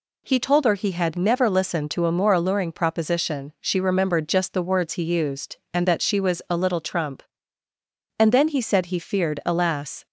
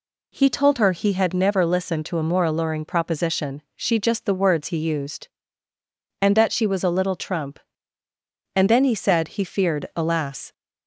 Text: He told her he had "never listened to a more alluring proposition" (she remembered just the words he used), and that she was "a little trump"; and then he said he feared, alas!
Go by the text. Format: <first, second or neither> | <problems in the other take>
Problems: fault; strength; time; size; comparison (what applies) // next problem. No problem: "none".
first | skips "remembered"; at 3.9 s